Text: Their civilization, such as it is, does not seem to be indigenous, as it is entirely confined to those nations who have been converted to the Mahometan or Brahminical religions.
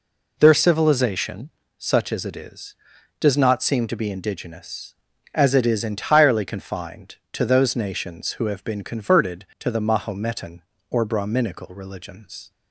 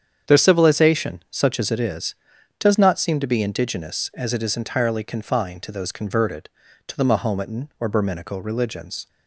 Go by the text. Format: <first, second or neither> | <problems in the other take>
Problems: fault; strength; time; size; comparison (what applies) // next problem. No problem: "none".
first | starts louder than the rest; strong; until 1.3 s; 8 dB // skips "nations who have been"; at 5.9 s